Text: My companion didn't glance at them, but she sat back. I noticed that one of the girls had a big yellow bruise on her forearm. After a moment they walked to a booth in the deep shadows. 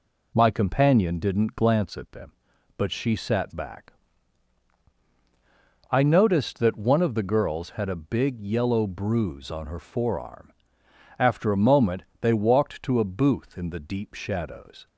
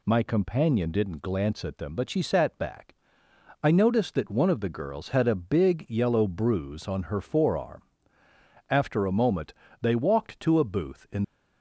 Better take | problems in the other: first | pauses between "moment" and "they"; slight; at 9.5 s; 0.26 s long; slight in the first // stops before "the deep shadows"; at 11.2 s

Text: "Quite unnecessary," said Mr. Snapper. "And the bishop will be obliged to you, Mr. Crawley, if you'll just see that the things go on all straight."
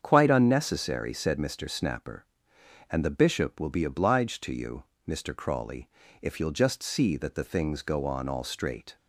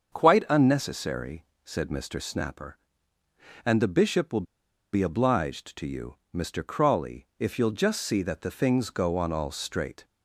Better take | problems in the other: first | starts louder than the rest; until 1.1 s; 7 dB; strong in the first // pauses between "will" and "be"; noticeable; at 4.4 s; 0.48 s long

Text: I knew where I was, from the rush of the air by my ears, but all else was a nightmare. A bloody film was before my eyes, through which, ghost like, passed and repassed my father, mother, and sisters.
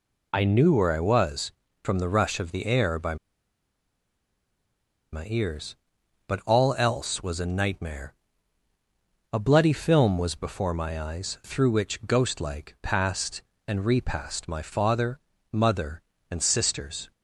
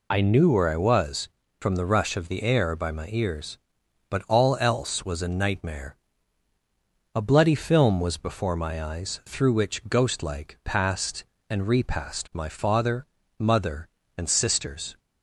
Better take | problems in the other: second | pauses between "by" and "my"; strong; at 3.1 s; 1.9 s long

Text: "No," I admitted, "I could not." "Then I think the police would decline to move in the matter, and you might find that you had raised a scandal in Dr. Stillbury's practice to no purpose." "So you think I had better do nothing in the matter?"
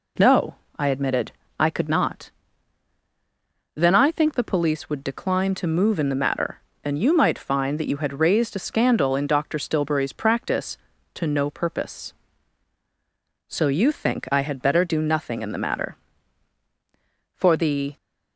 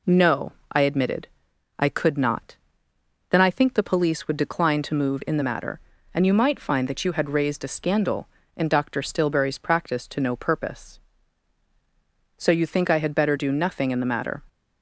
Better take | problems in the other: second | goes on to say "For the"; from 17.3 s on; 0.60 s long

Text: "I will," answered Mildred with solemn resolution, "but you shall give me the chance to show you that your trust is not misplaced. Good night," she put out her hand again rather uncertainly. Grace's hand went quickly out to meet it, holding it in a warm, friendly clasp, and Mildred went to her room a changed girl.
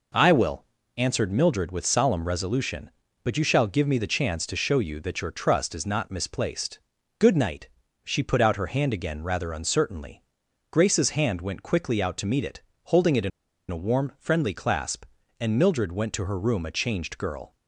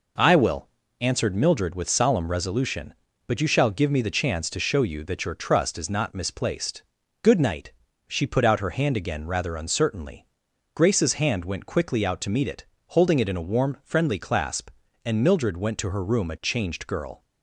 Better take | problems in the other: second | pauses between "in" and "a"; at 13.3 s; 0.41 s long

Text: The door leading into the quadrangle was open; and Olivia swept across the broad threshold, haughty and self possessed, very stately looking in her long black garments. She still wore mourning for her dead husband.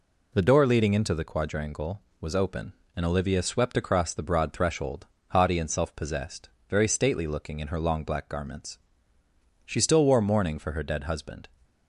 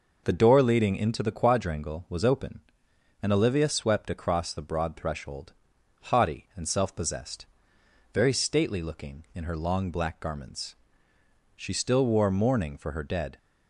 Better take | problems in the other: first | stops before "husband"; at 13.3 s

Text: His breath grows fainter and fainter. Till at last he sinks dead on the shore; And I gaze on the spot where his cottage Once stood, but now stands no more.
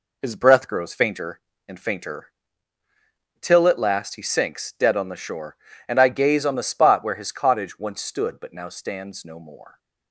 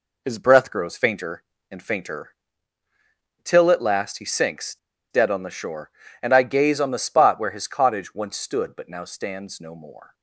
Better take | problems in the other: first | pauses between "sinks" and "dead"; slight; at 4.7 s; 0.34 s long

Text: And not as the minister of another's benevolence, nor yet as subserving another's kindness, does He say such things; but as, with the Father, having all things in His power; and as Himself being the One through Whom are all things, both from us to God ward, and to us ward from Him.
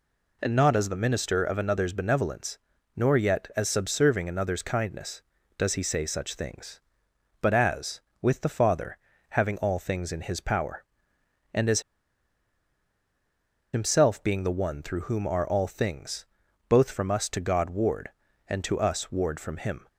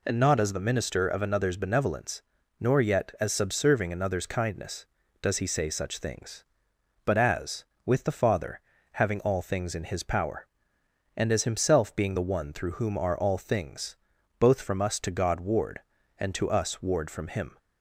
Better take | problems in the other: second | pauses between "as" and "Himself"; strong; at 11.8 s; 1.9 s long

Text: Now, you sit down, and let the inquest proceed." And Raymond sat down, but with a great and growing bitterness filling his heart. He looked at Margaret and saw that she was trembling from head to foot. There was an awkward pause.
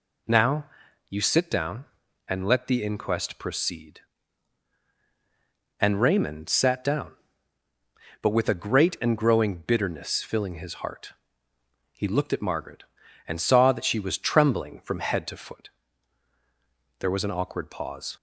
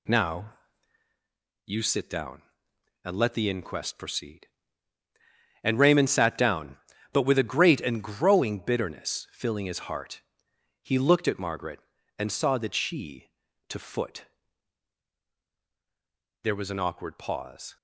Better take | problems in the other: first | skips "was trembling from head"; at 13.4 s

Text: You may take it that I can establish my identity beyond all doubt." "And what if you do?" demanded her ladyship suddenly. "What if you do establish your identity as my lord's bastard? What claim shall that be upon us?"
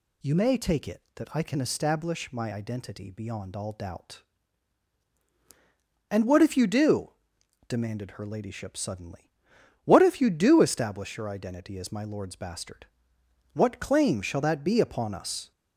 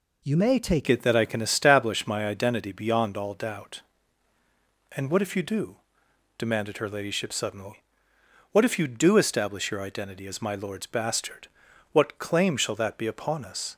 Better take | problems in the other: first | changes voice at "it"; from 0.8 s on; 12.9 s long

